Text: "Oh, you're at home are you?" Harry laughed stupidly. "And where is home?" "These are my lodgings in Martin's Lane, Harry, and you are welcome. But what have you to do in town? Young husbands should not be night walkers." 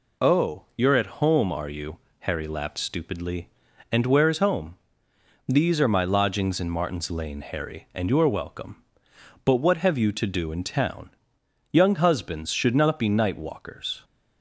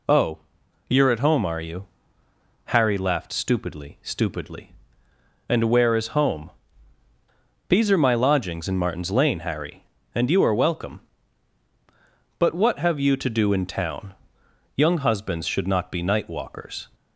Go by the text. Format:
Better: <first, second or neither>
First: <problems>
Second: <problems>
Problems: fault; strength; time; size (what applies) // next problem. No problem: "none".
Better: first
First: none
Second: says "stupidly" twice; at 4.0 s